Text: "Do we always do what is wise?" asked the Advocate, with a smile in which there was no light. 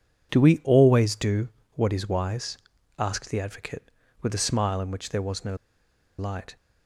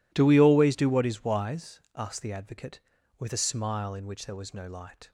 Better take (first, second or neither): second